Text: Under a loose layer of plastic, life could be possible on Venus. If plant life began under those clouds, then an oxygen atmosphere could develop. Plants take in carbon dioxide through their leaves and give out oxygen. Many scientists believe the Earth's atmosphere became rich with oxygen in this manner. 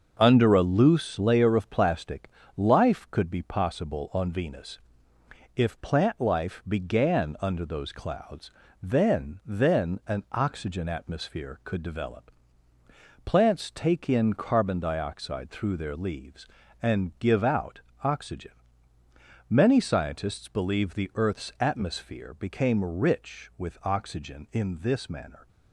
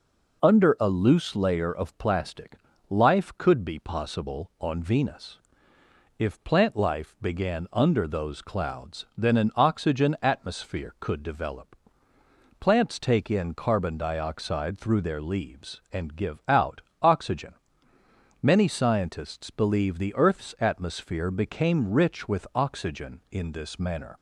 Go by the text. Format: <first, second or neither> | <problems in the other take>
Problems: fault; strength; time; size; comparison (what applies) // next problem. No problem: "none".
second | starts louder than the rest; until 1.2 s; 6 dB // says "then" twice; at 9.4 s // pauses between "out" and "oxygen"; slight; at 17.7 s; 0.22 s long; slight in the second